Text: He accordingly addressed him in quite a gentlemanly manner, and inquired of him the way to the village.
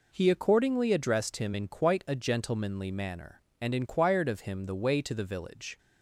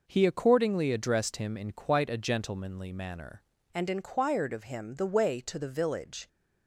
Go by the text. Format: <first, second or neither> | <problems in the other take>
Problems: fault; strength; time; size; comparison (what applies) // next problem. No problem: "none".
first | changes voice at "and"; from 3.7 s on; 2.5 s long